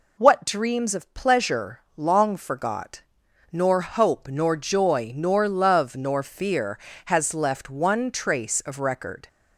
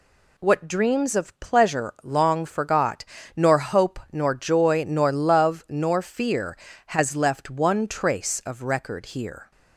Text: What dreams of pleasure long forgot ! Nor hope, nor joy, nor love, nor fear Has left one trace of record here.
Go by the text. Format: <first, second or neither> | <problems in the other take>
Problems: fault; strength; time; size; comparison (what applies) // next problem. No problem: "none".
second | stops before "here"; at 9.2 s